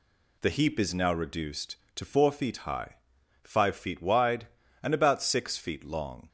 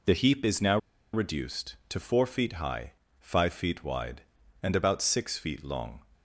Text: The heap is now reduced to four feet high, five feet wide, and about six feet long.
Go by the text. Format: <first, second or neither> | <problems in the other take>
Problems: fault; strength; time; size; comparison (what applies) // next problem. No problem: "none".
first | pauses between "now" and "reduced"; slight; at 0.7 s; 0.35 s long